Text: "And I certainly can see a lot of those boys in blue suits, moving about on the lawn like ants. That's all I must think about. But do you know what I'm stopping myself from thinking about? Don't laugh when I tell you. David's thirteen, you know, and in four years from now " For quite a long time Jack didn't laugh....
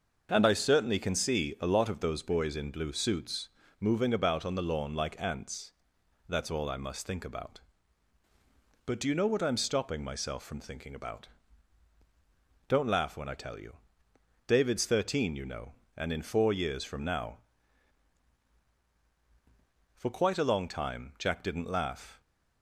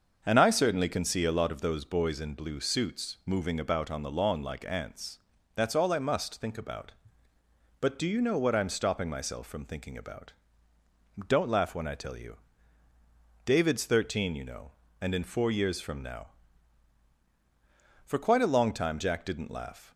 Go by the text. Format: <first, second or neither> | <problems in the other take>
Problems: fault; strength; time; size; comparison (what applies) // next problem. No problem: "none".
neither | starts louder than the rest; the same in both